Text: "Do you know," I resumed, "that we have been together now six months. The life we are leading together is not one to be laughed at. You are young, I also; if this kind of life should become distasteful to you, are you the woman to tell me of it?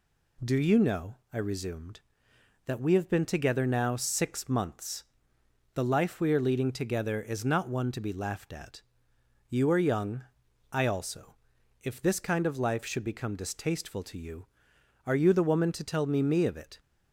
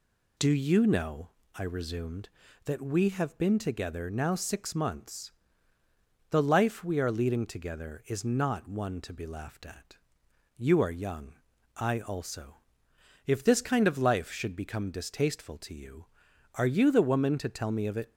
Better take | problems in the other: second | says "me" twice; at 16.2 s

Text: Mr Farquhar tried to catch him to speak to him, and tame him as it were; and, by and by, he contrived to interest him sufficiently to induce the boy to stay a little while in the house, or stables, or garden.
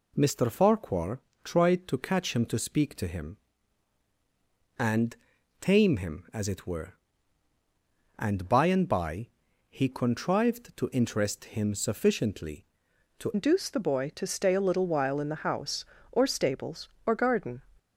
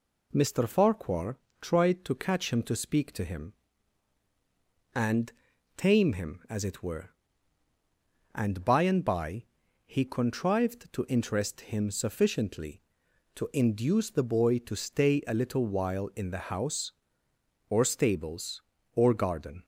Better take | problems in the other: second | pauses between "Farquhar" and "tried"; slight; at 1.1 s; 0.24 s long; slight in the second // pauses between "and" and "tame"; at 5.1 s; 0.44 s long; also in the second // changes voice at "induce"; from 13.3 s on; 4.3 s long

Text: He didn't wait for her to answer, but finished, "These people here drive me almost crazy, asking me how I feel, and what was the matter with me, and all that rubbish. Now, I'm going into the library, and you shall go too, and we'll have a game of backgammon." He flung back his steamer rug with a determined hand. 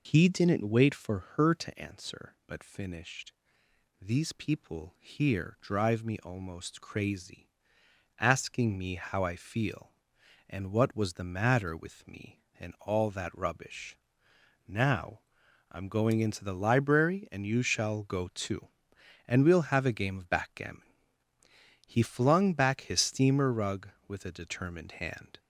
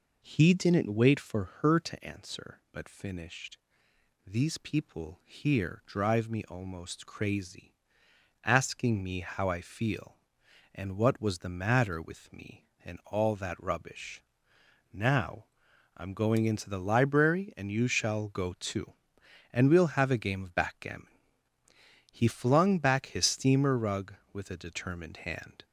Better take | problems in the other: second | loses the start of "He"; at 0.0 s; 60 ms // pauses between "for" and "her"; slight; at 1.1 s; 0.16 s long; slight in the second

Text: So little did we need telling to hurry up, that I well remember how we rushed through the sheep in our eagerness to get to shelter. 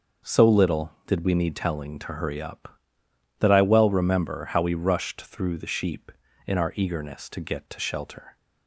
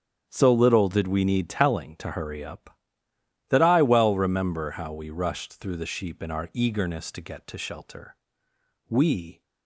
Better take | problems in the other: first | starts louder than the rest; strong; until 1.3 s; 8.5 dB // goes on to say "We"; from 8.8 s on; 0.54 s long

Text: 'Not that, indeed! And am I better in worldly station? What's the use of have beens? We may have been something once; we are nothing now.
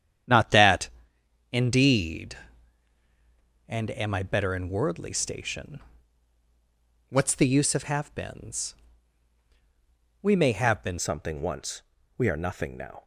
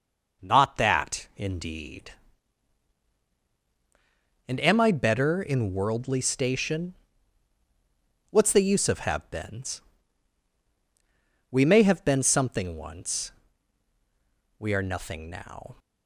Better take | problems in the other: second | starts louder than the rest; strong; until 1.8 s; 9.5 dB // changes voice at "something"; from 10.9 s on; 2.1 s long

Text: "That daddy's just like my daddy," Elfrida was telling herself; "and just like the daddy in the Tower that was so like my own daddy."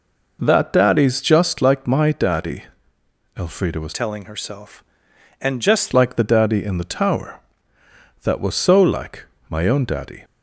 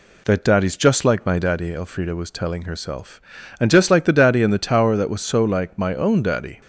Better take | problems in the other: second | changes voice from "telling" to "just"; from 3.9 to 5.9 s; 2.0 s long // pauses between "like" and "my"; slight; at 9.2 s; 0.24 s long

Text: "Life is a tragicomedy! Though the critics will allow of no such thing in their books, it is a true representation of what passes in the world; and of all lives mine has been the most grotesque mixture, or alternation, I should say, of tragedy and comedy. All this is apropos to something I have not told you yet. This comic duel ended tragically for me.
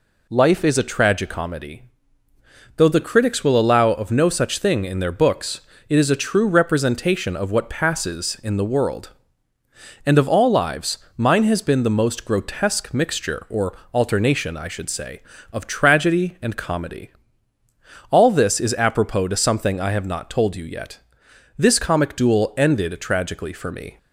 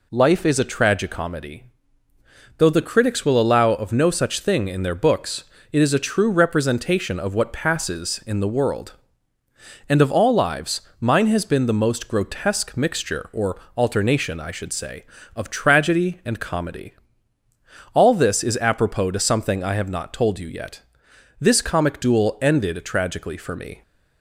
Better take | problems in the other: neither | pauses between "lives" and "mine"; slight; the same in both // pauses between "or" and "alternation"; slight; the same in both

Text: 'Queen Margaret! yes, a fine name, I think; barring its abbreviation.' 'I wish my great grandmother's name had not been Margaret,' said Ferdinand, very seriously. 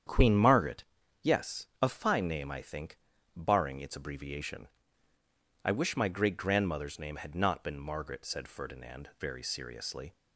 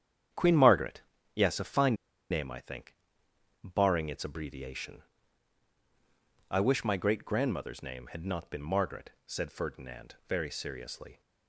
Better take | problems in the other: first | starts louder than the rest; strong; until 1.6 s; 9 dB; strong in the first // pauses between "fine" and "name"; at 1.9 s; 0.36 s long

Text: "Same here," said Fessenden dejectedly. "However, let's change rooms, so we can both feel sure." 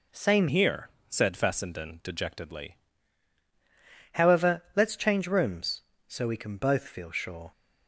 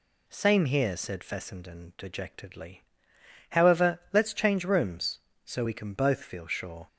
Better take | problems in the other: second | changes voice from "here" to "dejectedly"; from 0.4 to 2.7 s; 2.3 s long

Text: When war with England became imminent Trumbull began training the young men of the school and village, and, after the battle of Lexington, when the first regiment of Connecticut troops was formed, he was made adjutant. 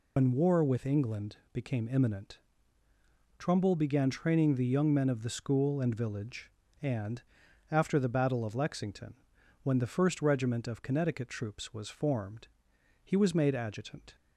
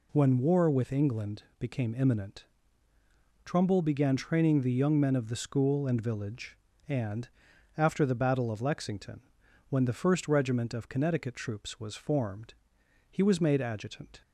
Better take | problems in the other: second | loses the start of "When"; at 0.1 s; 115 ms // pauses between "England" and "became"; slight; at 1.3 s; 0.16 s long; slight in the second // pauses between "imminent" and "Trumbull"; at 2.3 s; 1.0 s long; also in the second

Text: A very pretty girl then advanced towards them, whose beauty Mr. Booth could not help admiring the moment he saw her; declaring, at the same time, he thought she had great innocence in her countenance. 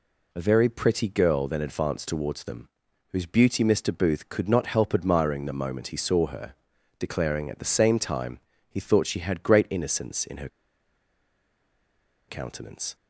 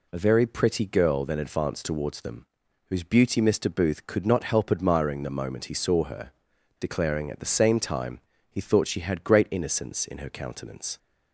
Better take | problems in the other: second | pauses between "her" and "countenance"; strong; at 10.4 s; 1.8 s long

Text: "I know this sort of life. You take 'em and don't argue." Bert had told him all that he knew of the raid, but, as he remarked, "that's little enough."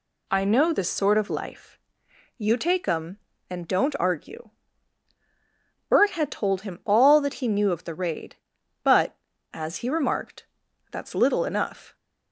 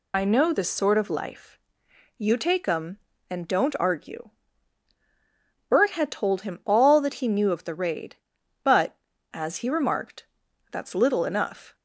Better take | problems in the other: first | loses the start of "I"; at 0.1 s; 50 ms

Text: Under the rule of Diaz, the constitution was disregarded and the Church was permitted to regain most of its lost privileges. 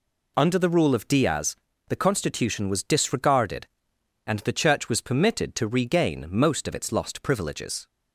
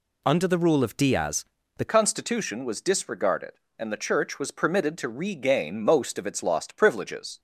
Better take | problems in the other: first | changes voice at "constitution"; from 1.8 s on; 5.5 s long

